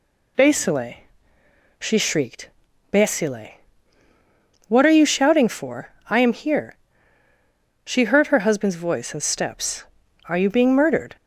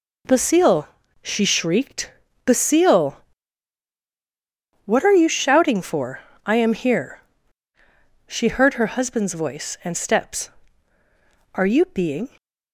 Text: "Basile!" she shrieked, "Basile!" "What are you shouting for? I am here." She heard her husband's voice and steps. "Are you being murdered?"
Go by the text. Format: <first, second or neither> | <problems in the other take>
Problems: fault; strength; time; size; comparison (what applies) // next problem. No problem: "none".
first | stops before "murdered"; at 12.3 s